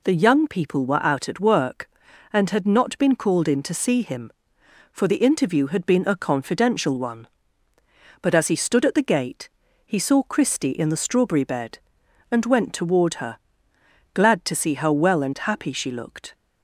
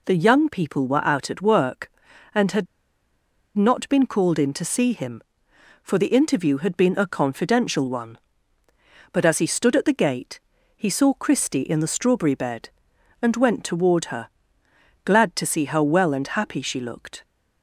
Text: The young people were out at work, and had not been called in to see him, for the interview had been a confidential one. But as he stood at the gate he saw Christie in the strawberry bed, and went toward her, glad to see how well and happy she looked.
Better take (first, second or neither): first